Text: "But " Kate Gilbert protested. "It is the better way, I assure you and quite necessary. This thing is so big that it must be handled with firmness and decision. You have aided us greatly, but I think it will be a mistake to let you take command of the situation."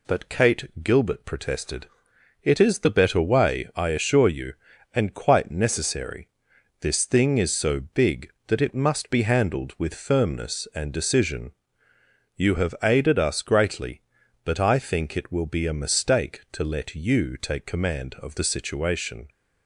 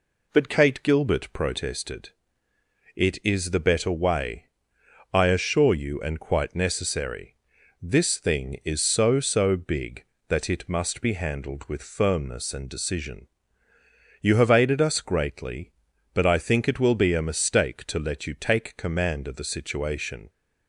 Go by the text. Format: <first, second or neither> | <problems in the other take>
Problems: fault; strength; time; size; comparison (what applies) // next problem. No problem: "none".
first | says "so" twice; at 9.1 s